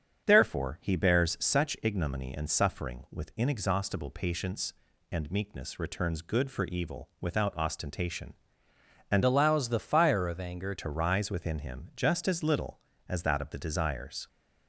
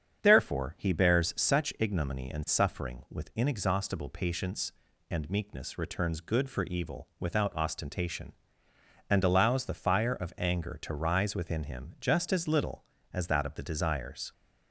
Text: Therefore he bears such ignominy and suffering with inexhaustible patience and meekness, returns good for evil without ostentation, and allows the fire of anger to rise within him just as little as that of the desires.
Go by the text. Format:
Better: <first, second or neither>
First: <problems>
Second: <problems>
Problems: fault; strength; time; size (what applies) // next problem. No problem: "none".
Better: second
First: starts louder than the rest; strong; until 1.3 s; 7.5 dB // changes voice from "allows" to "anger"; from 9.2 to 10.7 s; 1.5 s long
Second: starts louder than the rest; strong; until 1.2 s; 7.5 dB